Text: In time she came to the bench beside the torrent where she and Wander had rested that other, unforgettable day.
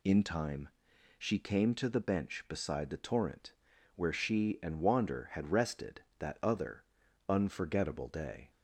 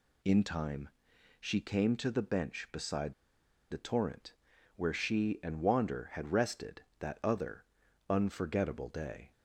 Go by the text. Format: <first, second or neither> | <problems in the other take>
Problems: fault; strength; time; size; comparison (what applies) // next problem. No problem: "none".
first | pauses between "time" and "she"; noticeable; at 0.8 s; 0.50 s long; noticeable in the first // pauses between "beside" and "the"; noticeable; at 3.1 s; 0.57 s long // pauses between "torrent" and "where"; at 4.3 s; 0.44 s long; also in the first